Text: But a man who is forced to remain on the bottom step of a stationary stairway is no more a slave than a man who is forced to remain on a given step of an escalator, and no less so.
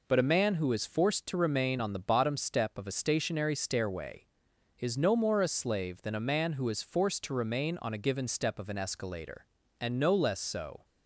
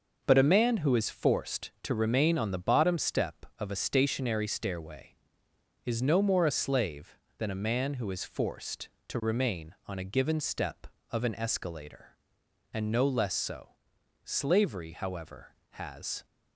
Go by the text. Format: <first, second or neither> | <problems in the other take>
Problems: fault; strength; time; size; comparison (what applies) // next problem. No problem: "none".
first | goes on to say "Slavery however has"; strong; from 14.2 s on; 2.0 s long